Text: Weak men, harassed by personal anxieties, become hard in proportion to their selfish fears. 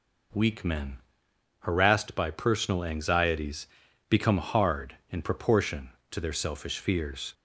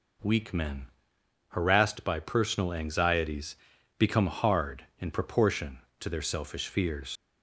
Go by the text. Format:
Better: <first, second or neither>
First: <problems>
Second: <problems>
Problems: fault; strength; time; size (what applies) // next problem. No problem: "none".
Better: first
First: none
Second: leaves "fears" unfinished; at 7.1 s; 70 ms